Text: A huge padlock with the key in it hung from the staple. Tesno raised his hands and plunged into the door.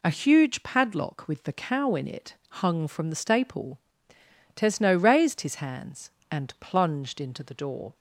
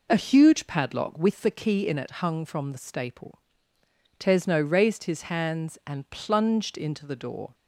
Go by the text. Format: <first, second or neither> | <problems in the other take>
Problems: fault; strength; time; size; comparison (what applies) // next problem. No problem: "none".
second | says "cow" for "key"; at 1.5 s // pauses between "it" and "hung"; slight; at 2.3 s; 0.16 s long